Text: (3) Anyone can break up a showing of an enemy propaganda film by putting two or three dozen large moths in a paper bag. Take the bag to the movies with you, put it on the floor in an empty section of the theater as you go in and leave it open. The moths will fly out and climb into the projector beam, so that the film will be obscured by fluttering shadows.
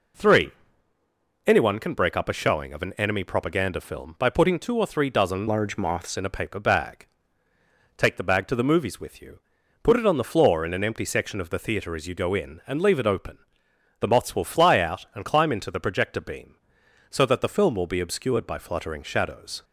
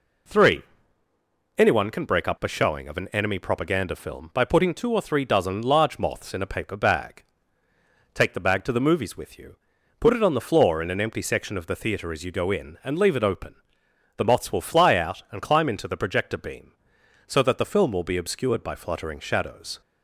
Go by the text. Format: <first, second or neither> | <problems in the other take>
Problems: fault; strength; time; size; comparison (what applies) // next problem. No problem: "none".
second | changes voice from "large" to "moths"; from 5.4 to 6.1 s; 0.7 s long